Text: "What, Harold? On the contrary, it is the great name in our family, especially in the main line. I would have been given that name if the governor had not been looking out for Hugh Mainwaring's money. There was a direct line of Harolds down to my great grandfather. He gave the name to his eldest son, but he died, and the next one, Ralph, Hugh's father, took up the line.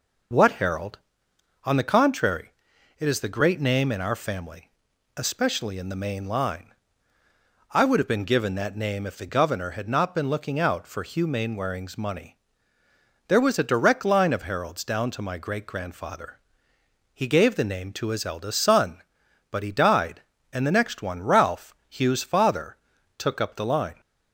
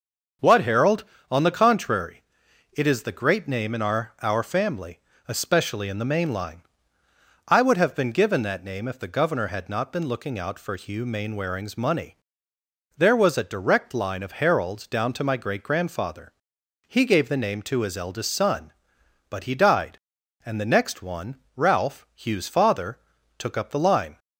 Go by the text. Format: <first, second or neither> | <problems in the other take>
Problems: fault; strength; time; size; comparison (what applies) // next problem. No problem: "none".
first | starts louder than the rest; until 1.6 s; 6.5 dB // says "our" twice; at 4.2 s